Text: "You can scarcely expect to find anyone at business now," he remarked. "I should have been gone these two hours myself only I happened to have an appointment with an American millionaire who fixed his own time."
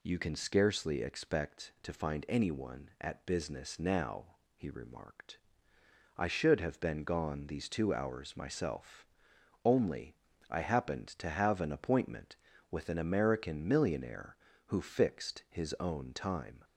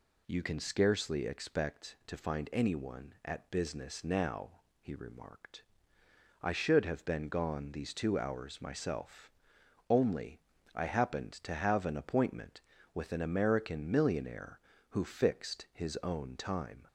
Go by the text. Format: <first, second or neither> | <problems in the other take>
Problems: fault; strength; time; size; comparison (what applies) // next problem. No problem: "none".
neither | pauses between "myself" and "only"; noticeable; the same in both // pauses between "only" and "I"; slight; the same in both